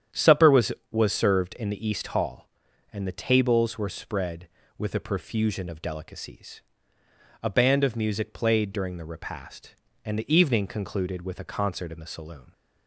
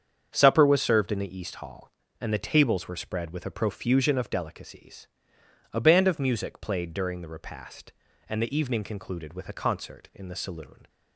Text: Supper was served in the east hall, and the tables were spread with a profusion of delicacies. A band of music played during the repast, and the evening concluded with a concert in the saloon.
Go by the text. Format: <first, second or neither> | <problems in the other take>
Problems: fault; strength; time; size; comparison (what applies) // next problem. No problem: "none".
second | starts louder than the rest; strong; until 1.3 s; 9.5 dB; strong in the second // says "was" twice; at 0.8 s